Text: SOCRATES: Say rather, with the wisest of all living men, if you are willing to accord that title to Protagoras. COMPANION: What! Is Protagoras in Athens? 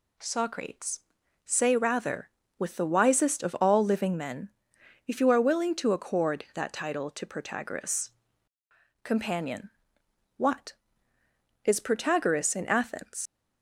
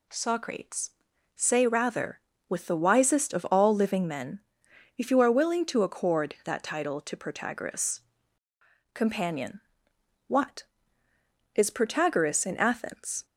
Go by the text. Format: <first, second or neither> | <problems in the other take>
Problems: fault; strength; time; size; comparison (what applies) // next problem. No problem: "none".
second | leaves "Athens" unfinished; at 13.2 s; 95 ms